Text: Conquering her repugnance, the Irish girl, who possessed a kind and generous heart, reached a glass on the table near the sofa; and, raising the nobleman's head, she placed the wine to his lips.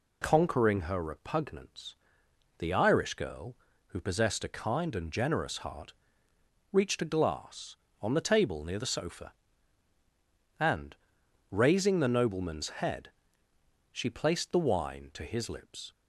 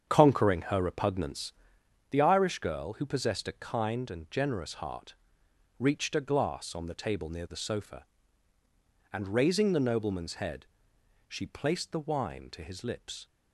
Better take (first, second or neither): first